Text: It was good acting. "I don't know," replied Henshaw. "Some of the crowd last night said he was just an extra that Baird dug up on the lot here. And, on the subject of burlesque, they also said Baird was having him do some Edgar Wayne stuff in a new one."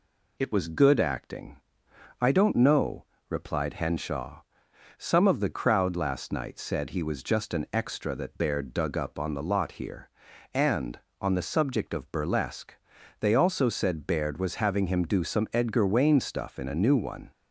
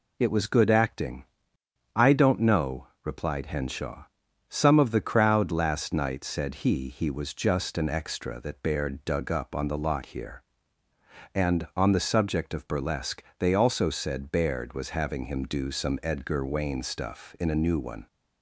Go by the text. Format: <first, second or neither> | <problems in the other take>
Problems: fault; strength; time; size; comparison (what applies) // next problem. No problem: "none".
first | says "he" twice; at 6.8 s